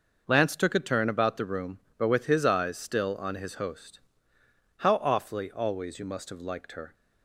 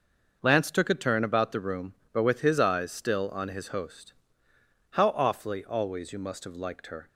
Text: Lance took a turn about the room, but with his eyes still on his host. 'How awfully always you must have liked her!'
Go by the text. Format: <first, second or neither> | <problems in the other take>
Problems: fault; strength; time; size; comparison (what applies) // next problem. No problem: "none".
neither | none